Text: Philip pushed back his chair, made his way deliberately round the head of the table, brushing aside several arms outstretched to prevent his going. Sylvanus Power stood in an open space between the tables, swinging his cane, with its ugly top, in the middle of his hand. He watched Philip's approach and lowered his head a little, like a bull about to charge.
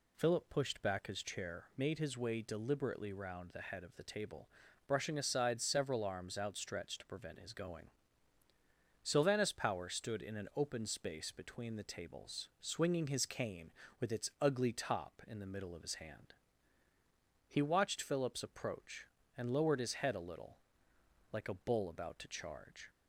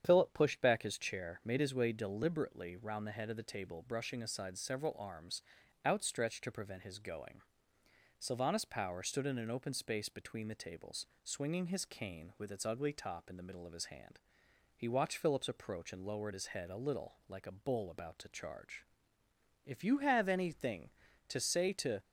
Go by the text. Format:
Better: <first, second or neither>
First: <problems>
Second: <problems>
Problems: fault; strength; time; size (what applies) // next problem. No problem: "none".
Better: first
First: none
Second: starts louder than the rest; strong; until 1.0 s; 8.5 dB // pauses between "arms" and "outstretched"; at 5.4 s; 0.42 s long // goes on to say "If you have anything to say to"; strong; from 19.6 s on; 2.3 s long